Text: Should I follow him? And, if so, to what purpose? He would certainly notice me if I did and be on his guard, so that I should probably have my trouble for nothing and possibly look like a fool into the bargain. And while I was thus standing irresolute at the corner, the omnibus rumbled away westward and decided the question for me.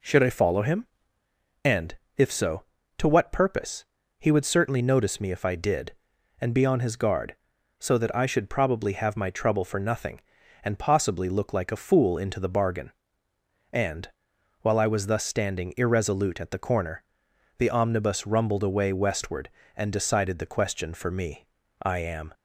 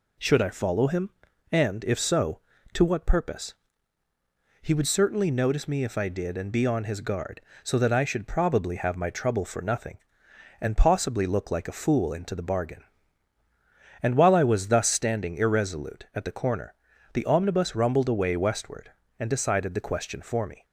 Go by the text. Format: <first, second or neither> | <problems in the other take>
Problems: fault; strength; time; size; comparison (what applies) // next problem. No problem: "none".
second | pauses between "And" and "while"; noticeable; at 14.0 s; 0.52 s long // goes on to say "I am"; from 21.8 s on; 0.50 s long